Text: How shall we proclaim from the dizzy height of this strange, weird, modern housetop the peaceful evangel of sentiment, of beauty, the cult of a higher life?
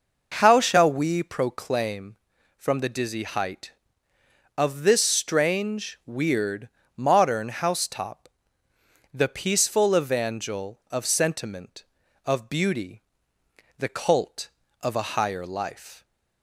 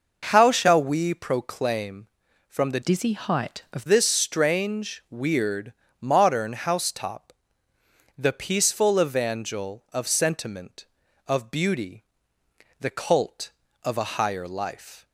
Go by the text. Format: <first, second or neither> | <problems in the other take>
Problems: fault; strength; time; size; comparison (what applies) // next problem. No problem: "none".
first | changes voice from "dizzy" to "of"; from 2.8 to 3.8 s; 1.0 s long // pauses between "housetop" and "the"; noticeable; at 7.3 s; 0.86 s long; noticeable in the first